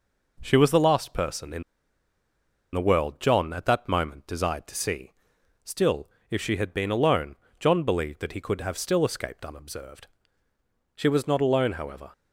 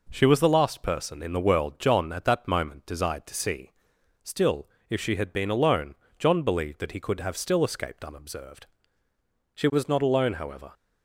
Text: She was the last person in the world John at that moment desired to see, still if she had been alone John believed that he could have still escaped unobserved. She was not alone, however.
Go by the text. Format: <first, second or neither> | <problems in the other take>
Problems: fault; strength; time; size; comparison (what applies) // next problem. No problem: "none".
second | pauses between "in" and "the"; at 1.6 s; 1.1 s long // pauses between "still" and "if"; slight; at 6.0 s; 0.22 s long; slight in the second // pauses between "alone" and "John"; slight; at 7.3 s; 0.22 s long; slight in the second